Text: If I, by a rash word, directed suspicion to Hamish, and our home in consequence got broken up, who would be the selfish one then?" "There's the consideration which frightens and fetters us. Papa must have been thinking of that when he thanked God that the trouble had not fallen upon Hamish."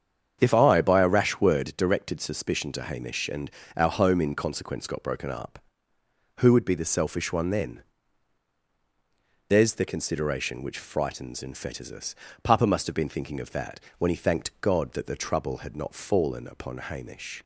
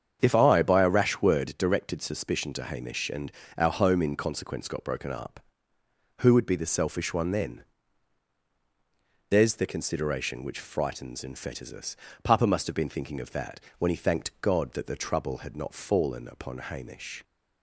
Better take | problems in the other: neither | starts louder than the rest; strong; the same in both // pauses between "and" and "our"; slight; the same in both // pauses between "that" and "when"; slight; the same in both

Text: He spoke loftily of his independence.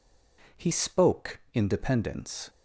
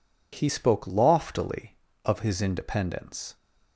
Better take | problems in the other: second | skips "loftily of his"; at 1.4 s

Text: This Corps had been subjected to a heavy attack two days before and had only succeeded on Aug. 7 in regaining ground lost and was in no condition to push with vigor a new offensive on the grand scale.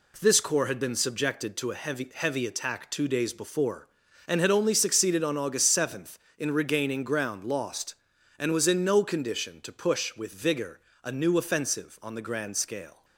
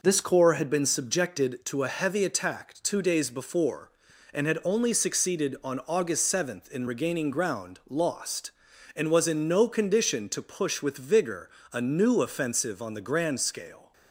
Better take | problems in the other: second | says "heavy" twice; at 2.1 s // pauses between "vigor" and "a"; slight; at 10.7 s; 0.24 s long; slight in the second

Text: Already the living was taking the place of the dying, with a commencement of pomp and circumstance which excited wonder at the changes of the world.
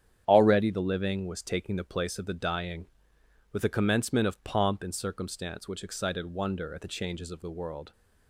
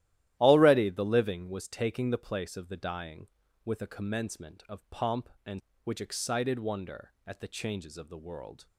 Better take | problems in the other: first | starts louder than the rest; strong; until 1.4 s; 13.5 dB; strong in the first // skips "circumstance"; at 5.7 s

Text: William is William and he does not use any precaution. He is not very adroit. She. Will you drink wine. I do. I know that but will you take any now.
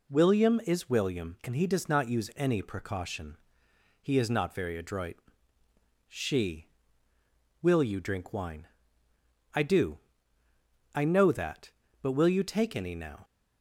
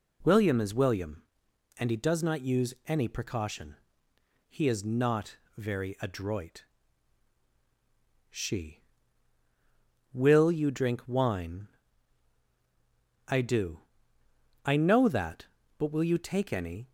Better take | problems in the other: first | pauses between "not" and "very"; slight; at 5.3 s; 0.20 s long // stops before "now"; at 16.8 s

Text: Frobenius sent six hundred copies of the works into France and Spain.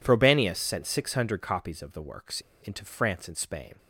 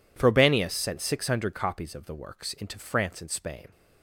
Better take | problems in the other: second | pauses between "works" and "into"; slight; at 2.4 s; 0.21 s long

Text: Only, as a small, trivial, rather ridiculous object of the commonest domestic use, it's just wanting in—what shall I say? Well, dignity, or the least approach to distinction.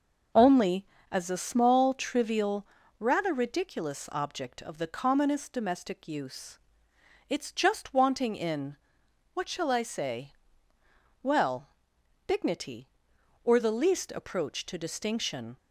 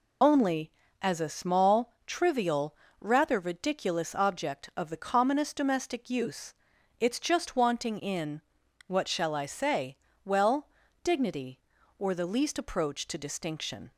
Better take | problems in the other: first | loses the start of "Only"; at 0.2 s; 40 ms

